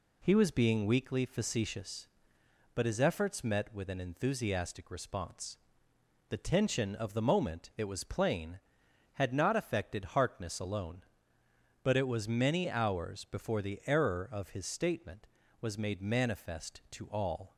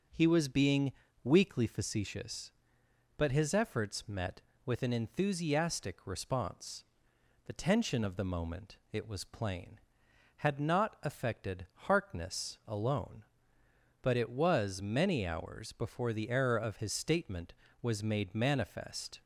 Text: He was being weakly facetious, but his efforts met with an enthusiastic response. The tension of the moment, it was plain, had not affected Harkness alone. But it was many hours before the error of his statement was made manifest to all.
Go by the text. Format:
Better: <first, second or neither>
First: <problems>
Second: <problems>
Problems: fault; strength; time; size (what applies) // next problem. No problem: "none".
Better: first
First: none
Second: starts louder than the rest; until 1.4 s; 6.5 dB // pauses between "being" and "weakly"; slight; at 0.9 s; 0.32 s long // pauses between "affected" and "Harkness"; slight; at 11.6 s; 0.18 s long // stops before "to all"; at 19.2 s